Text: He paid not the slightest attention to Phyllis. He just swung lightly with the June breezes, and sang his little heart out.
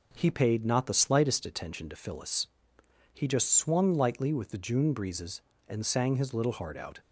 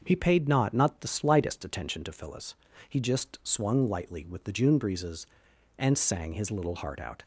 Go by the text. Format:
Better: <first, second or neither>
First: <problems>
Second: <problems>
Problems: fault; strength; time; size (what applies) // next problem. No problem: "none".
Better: first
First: none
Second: starts louder than the rest; until 1.0 s; 6.5 dB // says "not" twice; at 0.7 s